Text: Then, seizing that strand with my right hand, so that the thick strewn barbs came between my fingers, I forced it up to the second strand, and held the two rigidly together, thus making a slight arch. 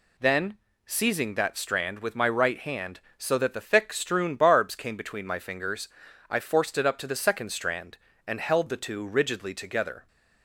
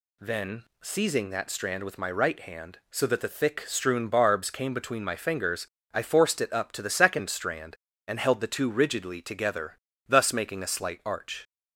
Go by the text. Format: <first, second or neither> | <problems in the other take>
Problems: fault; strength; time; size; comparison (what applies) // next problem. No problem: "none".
second | stops before "thus making a slight arch"; at 10.0 s